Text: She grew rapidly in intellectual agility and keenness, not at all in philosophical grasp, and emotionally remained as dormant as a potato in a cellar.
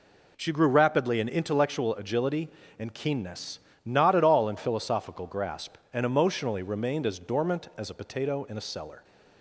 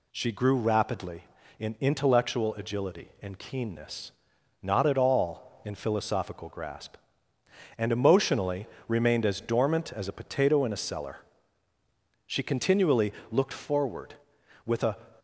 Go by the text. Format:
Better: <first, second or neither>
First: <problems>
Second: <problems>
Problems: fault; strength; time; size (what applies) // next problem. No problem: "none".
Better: first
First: none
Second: pauses between "emotionally" and "remained"; slight; at 8.6 s; 0.20 s long // goes on to say "She continually looked forward with a"; strong; from 12.2 s on; 2.7 s long